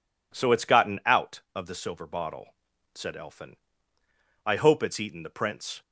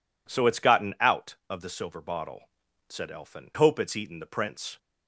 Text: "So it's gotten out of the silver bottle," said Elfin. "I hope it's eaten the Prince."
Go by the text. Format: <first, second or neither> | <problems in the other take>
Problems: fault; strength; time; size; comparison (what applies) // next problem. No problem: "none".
first | skips "I"; at 3.5 s